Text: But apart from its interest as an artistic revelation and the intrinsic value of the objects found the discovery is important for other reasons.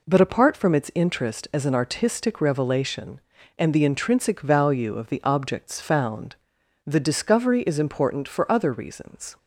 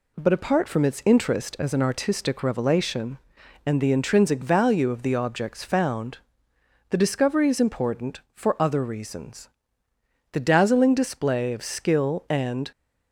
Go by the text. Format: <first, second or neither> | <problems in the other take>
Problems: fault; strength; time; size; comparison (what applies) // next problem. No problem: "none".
first | pauses between "found" and "the"; noticeable; at 6.1 s; 0.72 s long; noticeable in the first // goes on to say "The dazzling display of skill and"; strong; from 10.2 s on; 2.4 s long